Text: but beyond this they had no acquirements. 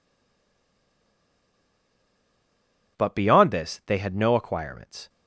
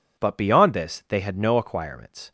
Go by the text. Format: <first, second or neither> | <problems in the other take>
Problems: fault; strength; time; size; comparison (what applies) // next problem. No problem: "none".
second | stays silent before the first word; strong; until 2.9 s; 2.9 s long